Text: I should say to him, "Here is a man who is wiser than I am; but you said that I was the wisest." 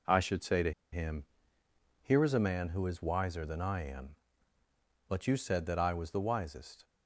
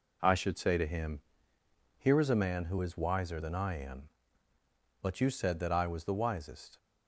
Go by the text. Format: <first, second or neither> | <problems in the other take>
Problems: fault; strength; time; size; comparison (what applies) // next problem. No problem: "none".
second | pauses between "to" and "him"; slight; at 0.7 s; 0.21 s long